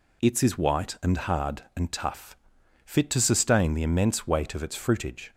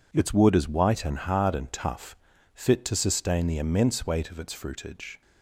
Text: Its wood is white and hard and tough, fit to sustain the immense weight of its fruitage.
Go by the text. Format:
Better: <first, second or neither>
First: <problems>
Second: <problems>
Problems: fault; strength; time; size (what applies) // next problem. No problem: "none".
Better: second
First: skips "wood"; at 0.4 s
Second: none